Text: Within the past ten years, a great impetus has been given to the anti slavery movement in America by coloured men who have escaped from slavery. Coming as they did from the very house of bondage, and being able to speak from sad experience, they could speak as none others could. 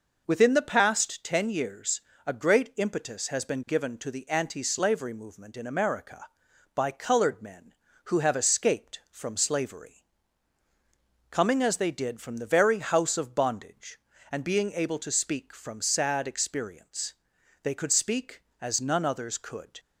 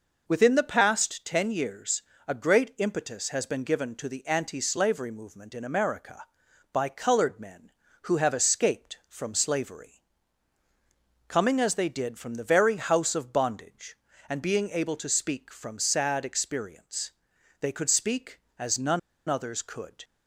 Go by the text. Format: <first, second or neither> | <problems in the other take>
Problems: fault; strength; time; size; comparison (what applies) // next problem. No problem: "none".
first | pauses between "none" and "others"; slight; at 18.9 s; 0.28 s long